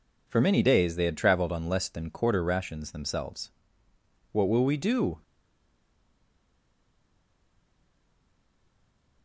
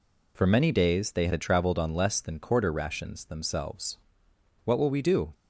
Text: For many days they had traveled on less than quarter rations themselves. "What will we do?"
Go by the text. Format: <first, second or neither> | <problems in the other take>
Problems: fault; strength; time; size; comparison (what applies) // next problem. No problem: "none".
second | stays silent after the last word; strong; from 5.2 s on; 4.0 s long